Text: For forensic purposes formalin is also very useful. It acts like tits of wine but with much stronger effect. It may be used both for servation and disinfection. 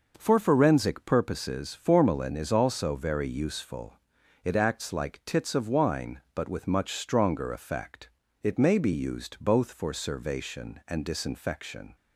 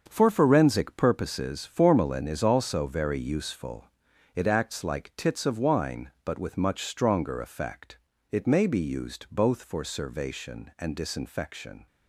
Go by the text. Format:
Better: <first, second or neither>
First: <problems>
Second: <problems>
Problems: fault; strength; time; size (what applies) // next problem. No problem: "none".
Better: first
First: none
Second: gets quieter; strong; throughout; 9.5 dB